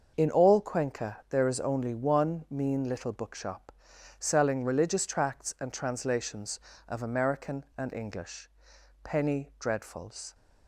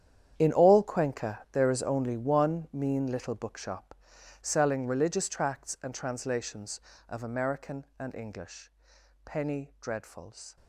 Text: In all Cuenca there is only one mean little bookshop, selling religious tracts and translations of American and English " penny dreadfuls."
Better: first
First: starts louder than the rest; until 1.1 s; 6.5 dB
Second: gets quieter; strong; throughout; 18.5 dB // starts louder than the rest; strong; until 1.3 s; 9.5 dB

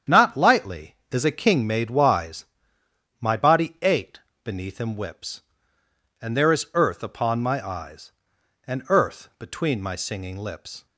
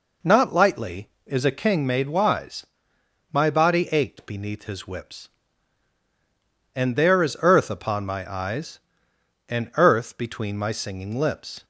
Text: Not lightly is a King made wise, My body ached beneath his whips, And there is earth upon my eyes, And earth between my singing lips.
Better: second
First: starts louder than the rest; strong; until 1.2 s; 8.5 dB // pauses between "ached" and "beneath"; slight; at 4.1 s; 0.22 s long // says "him" for "his"; at 4.7 s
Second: none

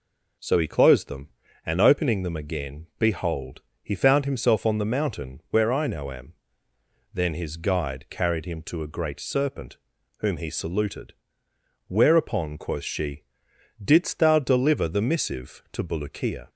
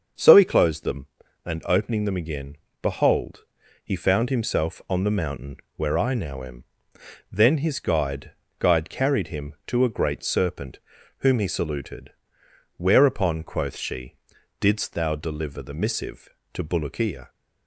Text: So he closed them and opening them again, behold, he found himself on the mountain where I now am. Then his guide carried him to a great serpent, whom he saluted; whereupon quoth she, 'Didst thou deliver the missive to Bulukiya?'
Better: first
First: none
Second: starts louder than the rest; until 1.5 s; 6.5 dB // pauses between "mountain" and "where"; slight; at 5.5 s; 0.20 s long // says "guide" twice; at 8.5 s

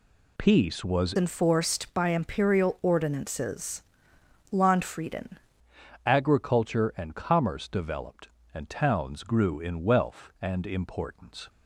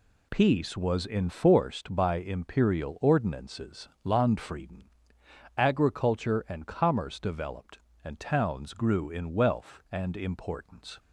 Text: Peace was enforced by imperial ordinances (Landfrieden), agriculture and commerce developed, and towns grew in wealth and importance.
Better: second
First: changes voice from "enforced" to "Landfrieden"; from 1.1 to 5.3 s; 4.2 s long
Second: none

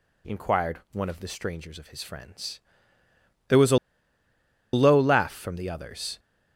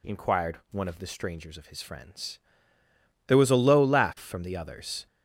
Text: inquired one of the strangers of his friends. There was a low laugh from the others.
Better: second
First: pauses between "a" and "low"; noticeable; at 3.7 s; 0.97 s long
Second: none

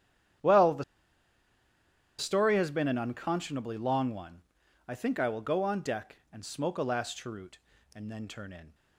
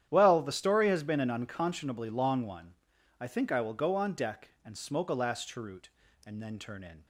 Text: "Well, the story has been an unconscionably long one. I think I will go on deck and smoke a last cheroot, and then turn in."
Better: second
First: starts louder than the rest; strong; until 2.7 s; 10 dB // pauses between "the" and "story"; strong; at 0.8 s; 1.3 s long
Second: starts louder than the rest; strong; until 1.1 s; 10 dB

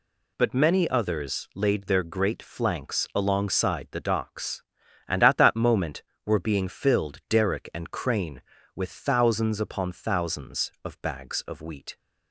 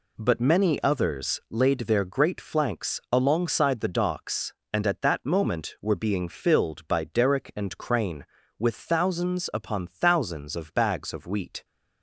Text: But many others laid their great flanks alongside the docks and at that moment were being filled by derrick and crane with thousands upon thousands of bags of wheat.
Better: second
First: skips "by"; at 7.2 s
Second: none

